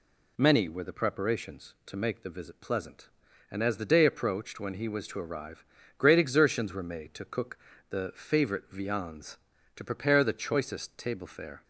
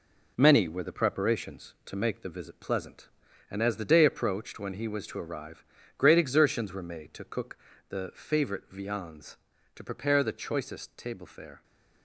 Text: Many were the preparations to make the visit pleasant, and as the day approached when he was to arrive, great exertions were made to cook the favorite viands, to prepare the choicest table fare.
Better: first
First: pauses between "cook" and "the"; slight; at 7.5 s; 0.30 s long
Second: gets quieter; throughout; 6 dB // pauses between "cook" and "the"; slight; at 7.5 s; 0.30 s long

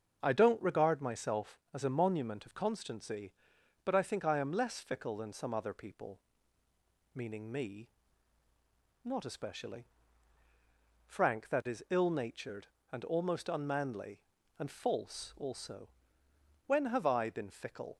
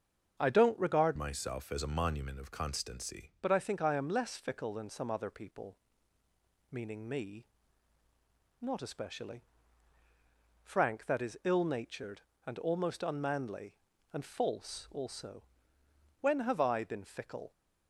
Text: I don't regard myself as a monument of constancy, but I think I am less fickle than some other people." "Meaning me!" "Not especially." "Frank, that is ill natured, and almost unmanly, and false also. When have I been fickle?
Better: first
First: starts louder than the rest; until 1.2 s; 6.5 dB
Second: starts louder than the rest; until 1.4 s; 6.5 dB // changes voice from "myself" to "constancy"; from 1.1 to 3.3 s; 2.2 s long

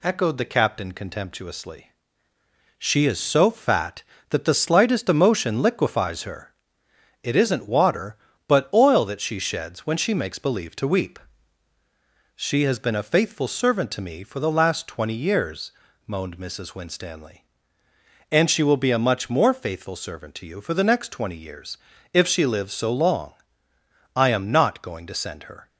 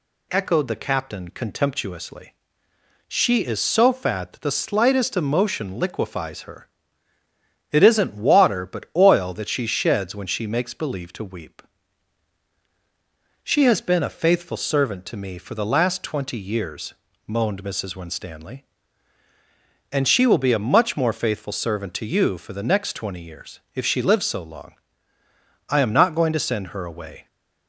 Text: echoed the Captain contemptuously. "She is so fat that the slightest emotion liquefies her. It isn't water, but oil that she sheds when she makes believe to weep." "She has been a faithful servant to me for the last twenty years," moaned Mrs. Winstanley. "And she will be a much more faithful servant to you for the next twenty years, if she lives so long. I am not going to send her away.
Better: second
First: stops before "away"; at 25.6 s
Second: none

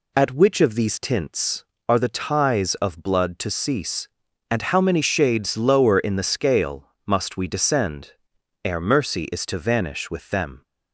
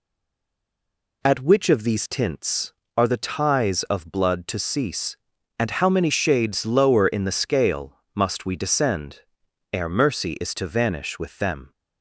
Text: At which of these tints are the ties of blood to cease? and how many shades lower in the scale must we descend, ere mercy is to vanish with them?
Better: first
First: pauses between "scale" and "must"; slight; at 6.9 s; 0.16 s long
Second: stays silent before the first word; noticeable; until 1.2 s; 1.2 s long // pauses between "scale" and "must"; slight; at 7.9 s; 0.16 s long

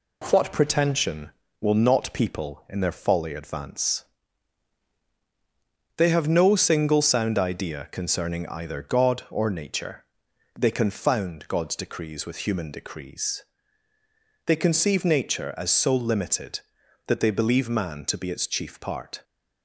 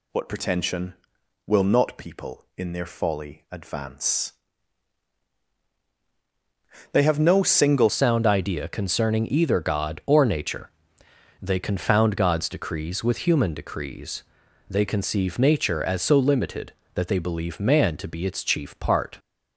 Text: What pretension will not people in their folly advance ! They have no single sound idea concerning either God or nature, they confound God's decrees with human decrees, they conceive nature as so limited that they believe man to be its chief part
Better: first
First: none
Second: changes voice at "sound"; from 7.8 s on; 11.3 s long

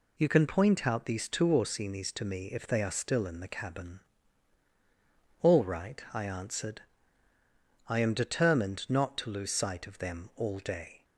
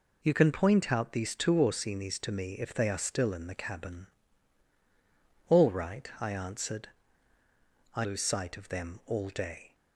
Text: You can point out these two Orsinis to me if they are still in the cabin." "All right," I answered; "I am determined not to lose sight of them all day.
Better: first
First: none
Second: skips "am determined not to"; at 8.0 s

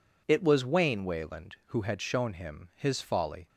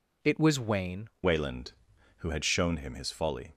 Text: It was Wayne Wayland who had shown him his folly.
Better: first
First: none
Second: changes voice at "Wayland"; from 1.2 s on; 2.3 s long

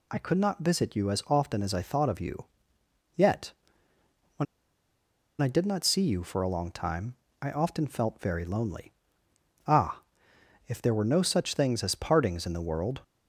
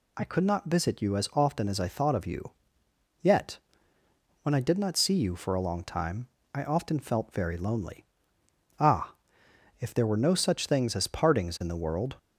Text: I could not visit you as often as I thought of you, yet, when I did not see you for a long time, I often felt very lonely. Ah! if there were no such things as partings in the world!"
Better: second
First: pauses between "when" and "I"; noticeable; at 4.4 s; 0.96 s long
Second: none

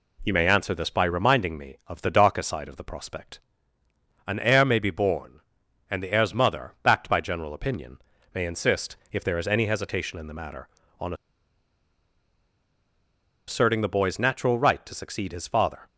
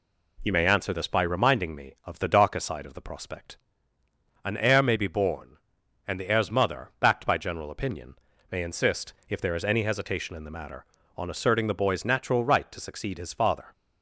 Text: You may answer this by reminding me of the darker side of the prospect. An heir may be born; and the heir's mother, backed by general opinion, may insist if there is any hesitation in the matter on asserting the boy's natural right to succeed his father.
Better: second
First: pauses between "insist" and "if"; slight; at 8.9 s; 0.16 s long // pauses between "on" and "asserting"; strong; at 11.1 s; 2.3 s long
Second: pauses between "insist" and "if"; slight; at 9.1 s; 0.16 s long

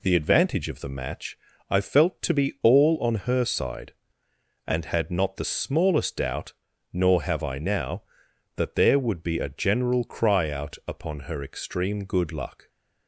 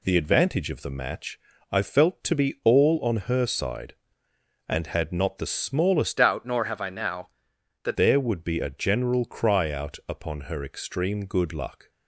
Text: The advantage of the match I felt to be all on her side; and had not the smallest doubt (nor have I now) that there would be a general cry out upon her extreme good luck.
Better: first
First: pauses between "match" and "I"; slight; at 1.3 s; 0.30 s long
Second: pauses between "match" and "I"; slight; at 1.3 s; 0.30 s long // changes voice from "doubt" to "that"; from 6.1 to 7.9 s; 1.8 s long

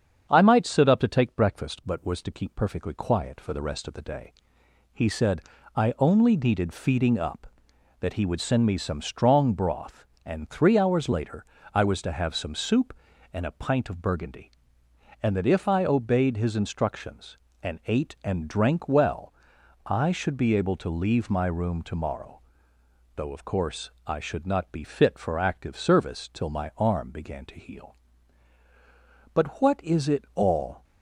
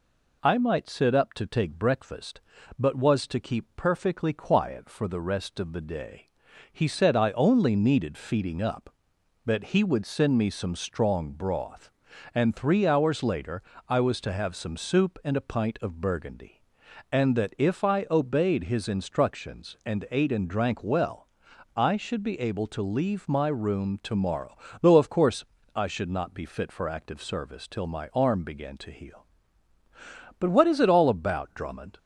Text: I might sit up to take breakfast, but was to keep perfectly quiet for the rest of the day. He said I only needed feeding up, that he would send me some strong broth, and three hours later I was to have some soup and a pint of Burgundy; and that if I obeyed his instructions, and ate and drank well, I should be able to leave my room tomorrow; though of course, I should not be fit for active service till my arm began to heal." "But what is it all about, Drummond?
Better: second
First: starts louder than the rest; strong; until 1.3 s; 7.5 dB // pauses between "said" and "I"; slight; at 5.4 s; 0.34 s long // pauses between "later" and "I"; slight; at 11.4 s; 0.30 s long // stops before "about Drummond"; at 30.8 s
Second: pauses between "later" and "I"; slight; at 13.6 s; 0.28 s long

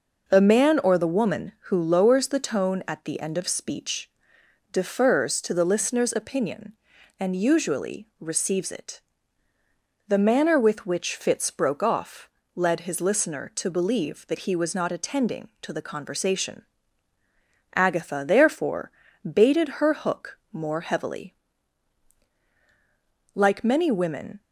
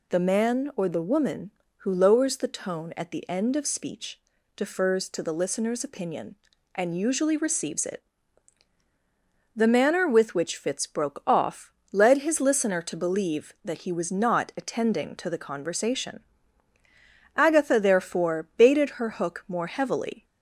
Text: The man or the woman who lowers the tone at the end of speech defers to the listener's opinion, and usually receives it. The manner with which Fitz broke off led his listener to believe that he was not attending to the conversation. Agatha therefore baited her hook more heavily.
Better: second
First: pauses between "speech" and "defers"; noticeable; at 4.1 s; 0.62 s long // pauses between "off" and "led"; slight; at 12.2 s; 0.26 s long // pauses between "therefore" and "baited"; at 18.9 s; 0.40 s long // goes on to say "Like many women"; noticeable; from 23.3 s on; 1.0 s long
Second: pauses between "speech" and "defers"; slight; at 4.2 s; 0.36 s long // pauses between "off" and "led"; slight; at 11.7 s; 0.20 s long

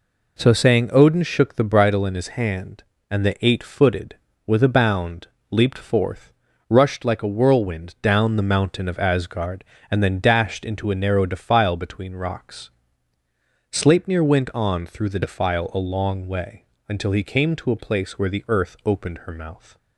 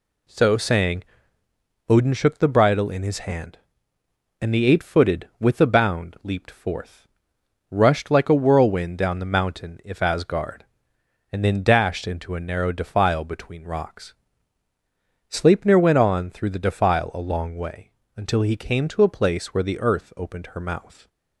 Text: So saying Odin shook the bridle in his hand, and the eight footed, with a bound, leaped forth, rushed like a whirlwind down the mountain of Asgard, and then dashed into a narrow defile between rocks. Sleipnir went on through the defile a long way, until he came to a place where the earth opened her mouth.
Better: first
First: none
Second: pauses between "saying" and "Odin"; noticeable; at 1.0 s; 0.84 s long // says "if" for "of"; at 9.8 s

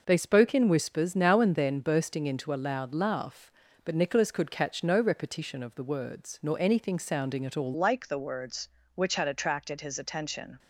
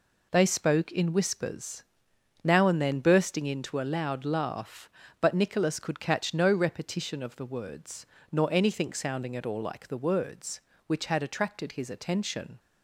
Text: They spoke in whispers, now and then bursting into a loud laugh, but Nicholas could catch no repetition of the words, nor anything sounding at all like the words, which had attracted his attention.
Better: second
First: changes voice at "like"; from 7.7 s on; 2.8 s long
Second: none

